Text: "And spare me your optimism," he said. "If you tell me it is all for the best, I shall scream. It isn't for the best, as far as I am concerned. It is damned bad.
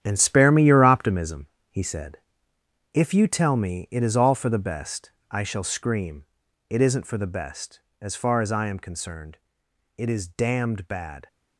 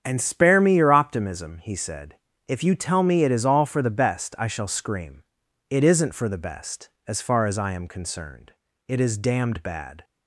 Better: second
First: gets quieter; strong; throughout; 11 dB // starts louder than the rest; strong; until 1.0 s; 10 dB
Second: starts louder than the rest; strong; until 1.0 s; 8 dB

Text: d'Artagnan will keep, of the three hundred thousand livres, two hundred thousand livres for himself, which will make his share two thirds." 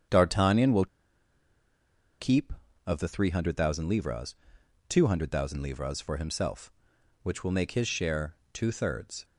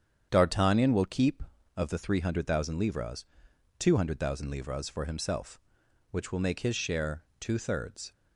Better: second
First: starts louder than the rest; strong; until 2.4 s; 8 dB // pauses between "will" and "keep"; strong; at 0.8 s; 1.3 s long // pauses between "share" and "two"; slight; at 8.3 s; 0.18 s long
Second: starts louder than the rest; strong; until 1.3 s; 8 dB // pauses between "share" and "two"; slight; at 7.2 s; 0.16 s long

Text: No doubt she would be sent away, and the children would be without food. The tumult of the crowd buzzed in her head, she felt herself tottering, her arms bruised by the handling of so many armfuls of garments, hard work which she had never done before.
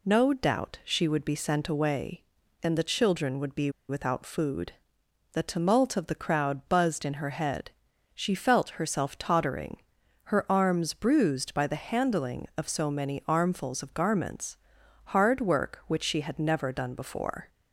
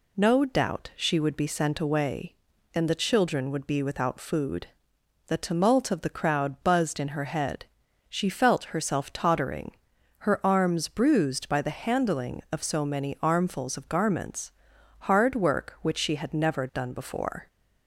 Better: second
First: pauses between "be" and "without"; slight; at 3.6 s; 0.19 s long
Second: none

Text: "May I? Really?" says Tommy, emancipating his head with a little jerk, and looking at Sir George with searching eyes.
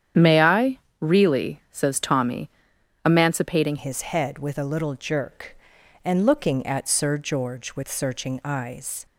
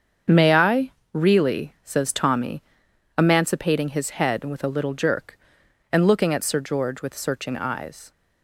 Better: second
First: starts louder than the rest; strong; until 1.3 s; 9 dB // changes voice at "his"; from 3.7 s on; 5.3 s long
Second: starts louder than the rest; until 1.4 s; 7 dB

